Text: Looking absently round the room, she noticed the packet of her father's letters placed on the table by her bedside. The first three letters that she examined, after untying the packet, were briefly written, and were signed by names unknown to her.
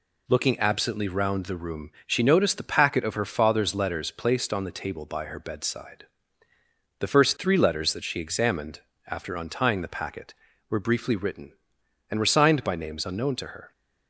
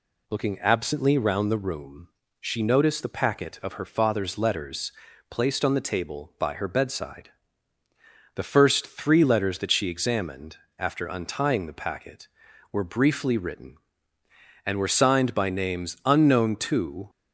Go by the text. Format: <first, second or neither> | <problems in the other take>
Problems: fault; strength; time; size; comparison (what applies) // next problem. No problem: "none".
first | pauses between "letters" and "placed"; at 4.9 s; 0.40 s long // stops before "her"; at 17.0 s